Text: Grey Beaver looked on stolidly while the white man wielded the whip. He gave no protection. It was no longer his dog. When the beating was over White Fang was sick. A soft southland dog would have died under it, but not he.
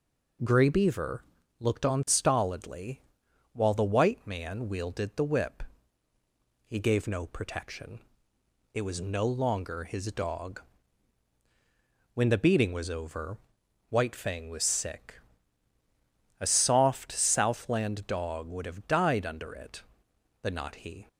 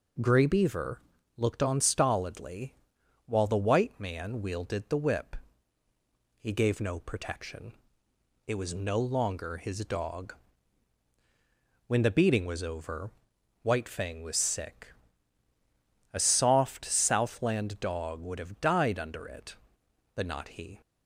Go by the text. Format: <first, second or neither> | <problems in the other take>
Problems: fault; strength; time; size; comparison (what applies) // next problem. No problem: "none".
neither | pauses between "Beaver" and "looked"; the same in both // pauses between "stolidly" and "while"; noticeable; the same in both // pauses between "over" and "White"; noticeable; the same in both